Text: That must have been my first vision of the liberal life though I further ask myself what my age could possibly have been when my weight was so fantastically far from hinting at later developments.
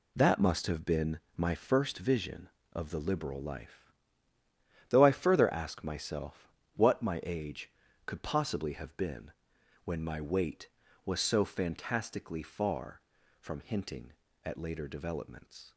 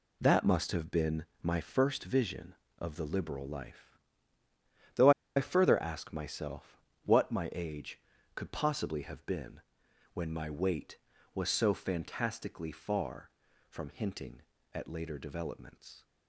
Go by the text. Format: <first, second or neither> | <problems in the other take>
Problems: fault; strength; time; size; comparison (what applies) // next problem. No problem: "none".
first | pauses between "been" and "my"; slight; at 1.2 s; 0.16 s long; slight in the first // pauses between "life" and "though"; noticeable; at 3.9 s; 0.96 s long; noticeable in the first // pauses between "though" and "I"; slight; at 5.1 s; 0.25 s long // pauses between "myself" and "what"; slight; at 6.7 s; 0.24 s long; slight in the first // pauses between "been" and "when"; noticeable; at 9.5 s; 0.54 s long; noticeable in the first